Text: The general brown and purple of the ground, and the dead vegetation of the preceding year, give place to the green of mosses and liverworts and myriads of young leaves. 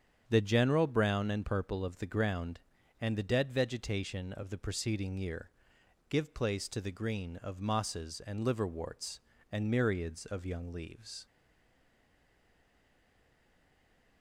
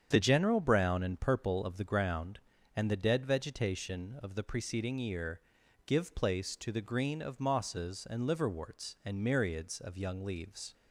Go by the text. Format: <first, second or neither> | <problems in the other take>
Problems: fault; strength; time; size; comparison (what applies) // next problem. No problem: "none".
second | starts louder than the rest; strong; until 1.2 s; 8 dB; strong in the second // stays silent after the last word; strong; from 11.2 s on; 3.0 s long